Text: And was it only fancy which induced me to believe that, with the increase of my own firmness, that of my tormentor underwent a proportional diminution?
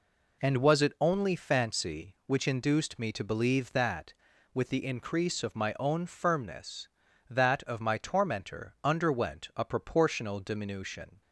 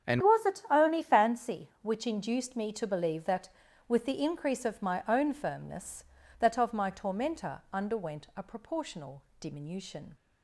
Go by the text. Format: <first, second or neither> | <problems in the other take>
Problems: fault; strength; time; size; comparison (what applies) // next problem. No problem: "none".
first | starts louder than the rest; strong; until 1.1 s; 8.5 dB // changes voice at "was"; from 0.2 s on; 9.9 s long // pauses between "proportional" and "diminution"; slight; at 9.2 s; 0.18 s long